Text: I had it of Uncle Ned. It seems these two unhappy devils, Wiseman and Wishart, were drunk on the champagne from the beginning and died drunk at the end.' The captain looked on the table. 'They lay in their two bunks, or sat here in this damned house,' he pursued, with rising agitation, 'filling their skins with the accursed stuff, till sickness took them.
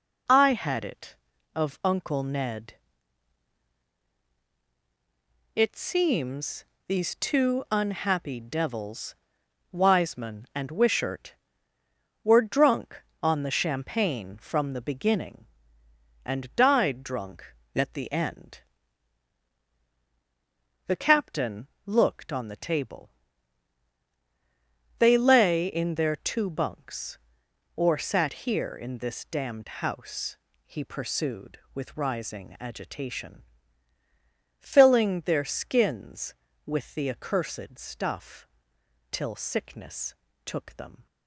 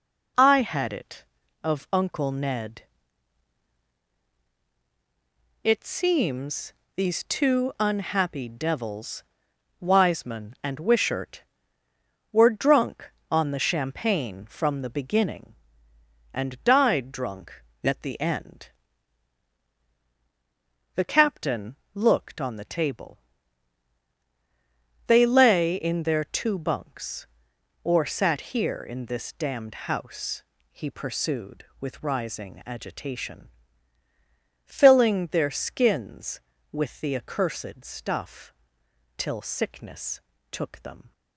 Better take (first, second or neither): neither